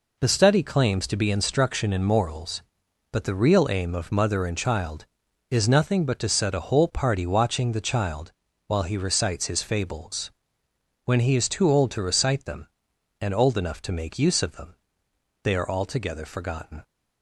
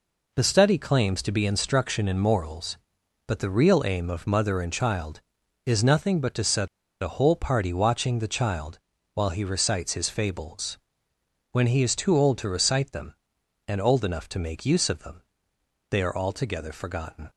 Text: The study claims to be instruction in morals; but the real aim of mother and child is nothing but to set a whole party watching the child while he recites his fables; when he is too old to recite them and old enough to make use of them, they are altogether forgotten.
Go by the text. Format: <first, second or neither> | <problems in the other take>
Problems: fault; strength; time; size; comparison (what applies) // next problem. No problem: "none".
first | pauses between "set" and "a"; slight; at 6.6 s; 0.35 s long // pauses between "child" and "while"; slight; at 8.7 s; 0.34 s long; slight in the first